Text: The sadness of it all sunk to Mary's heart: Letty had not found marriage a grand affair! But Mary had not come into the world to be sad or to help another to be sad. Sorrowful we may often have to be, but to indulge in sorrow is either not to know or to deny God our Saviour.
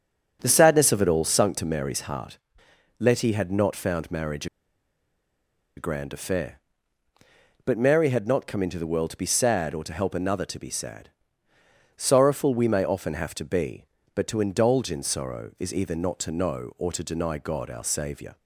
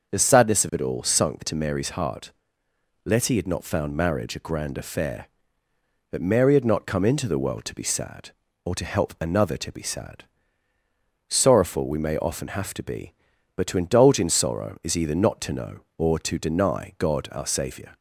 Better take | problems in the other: second | starts louder than the rest; strong; until 1.4 s; 7 dB; also in the second // pauses between "marriage" and "a"; strong; at 4.4 s; 1.3 s long

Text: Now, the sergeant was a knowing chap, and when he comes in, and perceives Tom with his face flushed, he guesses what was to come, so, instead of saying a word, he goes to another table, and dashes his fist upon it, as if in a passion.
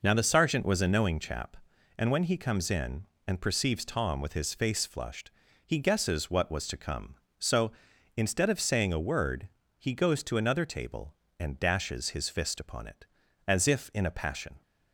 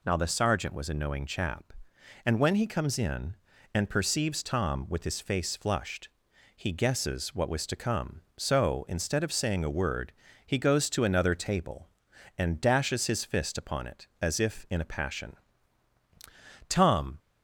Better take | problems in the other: first | goes on to say "Tom"; from 16.6 s on; 0.50 s long

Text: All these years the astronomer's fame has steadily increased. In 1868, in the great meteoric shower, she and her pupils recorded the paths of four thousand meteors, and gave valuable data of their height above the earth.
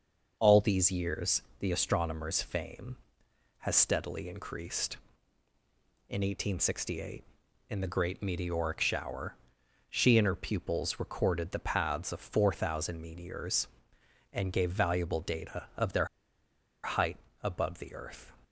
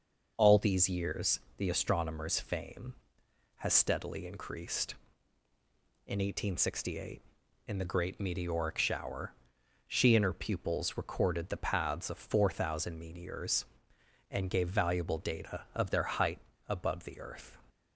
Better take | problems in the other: second | pauses between "years" and "the"; slight; at 1.4 s; 0.18 s long; slight in the second // pauses between "their" and "height"; noticeable; at 16.0 s; 0.78 s long // pauses between "height" and "above"; slight; at 17.1 s; 0.26 s long; slight in the second

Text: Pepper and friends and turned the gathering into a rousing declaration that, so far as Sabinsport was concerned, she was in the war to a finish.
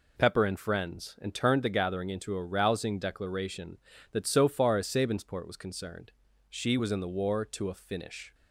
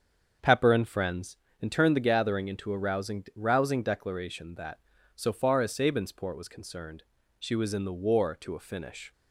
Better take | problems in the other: first | starts louder than the rest; until 1.6 s; 7 dB // says "rousing" twice; at 3.3 s

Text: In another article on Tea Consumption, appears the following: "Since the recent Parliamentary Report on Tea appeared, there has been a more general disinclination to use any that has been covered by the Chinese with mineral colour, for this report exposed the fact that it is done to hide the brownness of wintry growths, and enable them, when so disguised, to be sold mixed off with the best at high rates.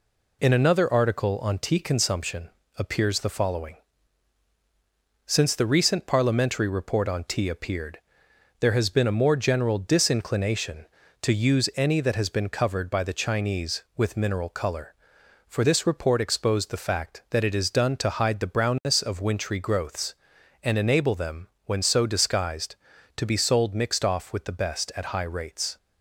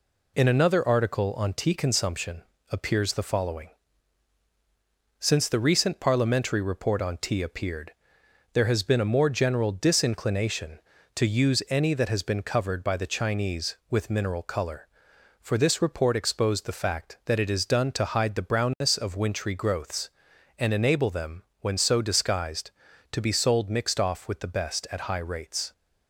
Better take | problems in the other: neither | none

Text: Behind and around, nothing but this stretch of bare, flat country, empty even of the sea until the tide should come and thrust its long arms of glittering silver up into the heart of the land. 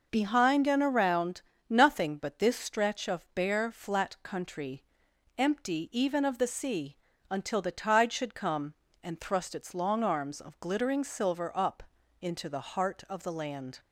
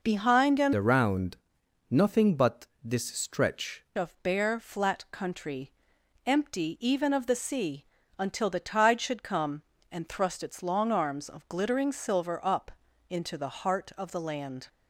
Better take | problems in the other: first | changes voice from "around" to "stretch"; from 0.7 to 3.8 s; 3.1 s long // pauses between "but" and "this"; slight; at 2.6 s; 0.18 s long // pauses between "sea" and "until"; slight; at 7.8 s; 0.32 s long; slight in the first // pauses between "up" and "into"; at 12.6 s; 0.38 s long; also in the first

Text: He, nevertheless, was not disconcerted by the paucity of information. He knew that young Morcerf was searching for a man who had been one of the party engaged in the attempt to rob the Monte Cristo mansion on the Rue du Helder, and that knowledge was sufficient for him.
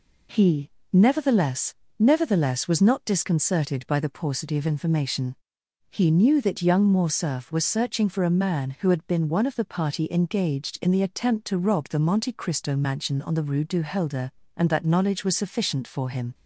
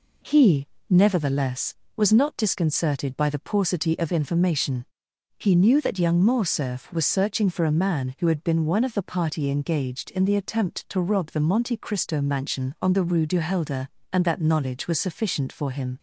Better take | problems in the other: second | says "nevertheless" twice; at 1.9 s

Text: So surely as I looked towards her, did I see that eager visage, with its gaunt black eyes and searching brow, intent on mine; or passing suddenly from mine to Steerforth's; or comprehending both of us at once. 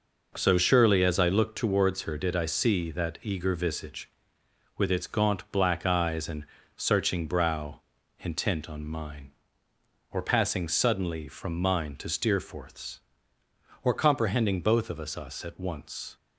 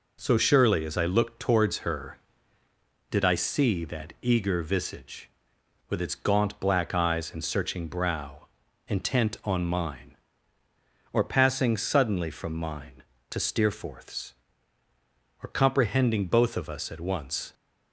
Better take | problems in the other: second | pauses between "and" and "searching"; slight; at 6.4 s; 0.32 s long // says "us" twice; at 15.1 s

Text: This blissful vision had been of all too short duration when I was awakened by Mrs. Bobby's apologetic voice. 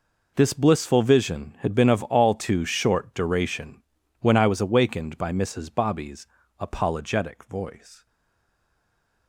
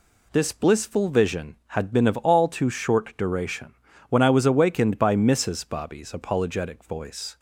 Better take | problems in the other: second | pauses between "duration" and "when"; at 3.8 s; 0.38 s long; also in the second // pauses between "Bobby's" and "apologetic"; slight; at 6.2 s; 0.32 s long // stays silent after the last word; noticeable; from 8.0 s on; 1.2 s long

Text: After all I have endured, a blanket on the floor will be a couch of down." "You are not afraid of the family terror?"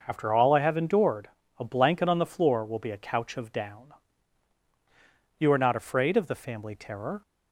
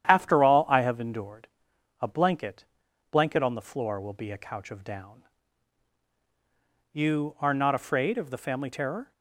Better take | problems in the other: first | starts louder than the rest; strong; until 1.1 s; 10 dB // says "blanket" twice; at 3.0 s

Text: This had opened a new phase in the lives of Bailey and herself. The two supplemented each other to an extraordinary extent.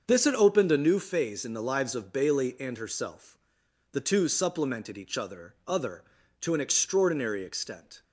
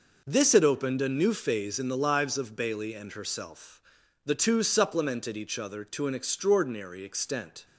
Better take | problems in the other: second | starts louder than the rest; until 1.0 s; 6.5 dB // says "other" twice; at 5.6 s

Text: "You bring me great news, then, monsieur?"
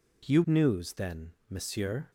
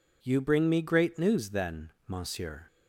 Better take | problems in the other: second | skips "bring me great"; at 0.4 s

